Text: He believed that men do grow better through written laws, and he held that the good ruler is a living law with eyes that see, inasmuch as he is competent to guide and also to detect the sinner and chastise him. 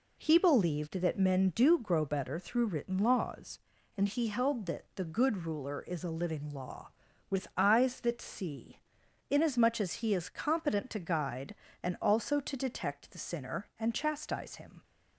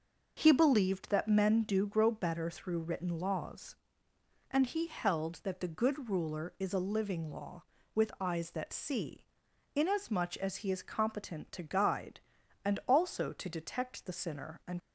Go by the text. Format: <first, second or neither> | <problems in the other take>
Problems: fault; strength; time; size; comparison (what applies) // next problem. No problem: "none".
first | stops before "chastise him"; at 14.7 s